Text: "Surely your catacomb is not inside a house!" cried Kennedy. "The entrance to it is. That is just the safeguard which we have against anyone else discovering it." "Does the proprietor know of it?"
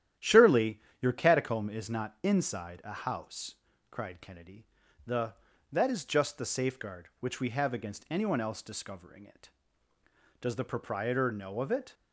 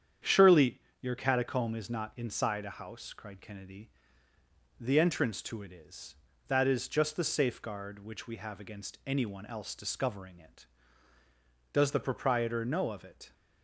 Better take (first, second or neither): second